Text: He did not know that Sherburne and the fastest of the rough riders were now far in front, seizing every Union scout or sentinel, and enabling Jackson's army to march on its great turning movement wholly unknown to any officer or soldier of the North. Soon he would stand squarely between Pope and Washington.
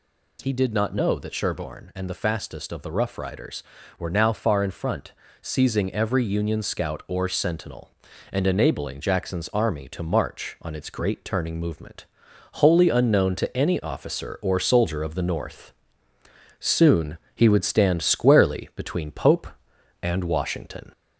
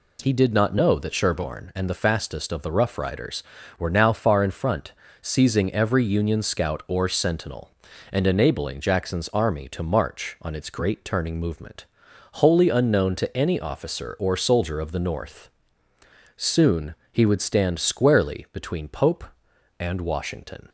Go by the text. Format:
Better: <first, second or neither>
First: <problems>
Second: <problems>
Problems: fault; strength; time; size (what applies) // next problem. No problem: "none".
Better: second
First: gets louder; slight; throughout; 2.5 dB // pauses between "movement" and "wholly"; noticeable; at 12.0 s; 0.48 s long // pauses between "Soon" and "he"; slight; at 17.1 s; 0.18 s long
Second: pauses between "movement" and "wholly"; noticeable; at 11.8 s; 0.48 s long // pauses between "Soon" and "he"; slight; at 16.9 s; 0.18 s long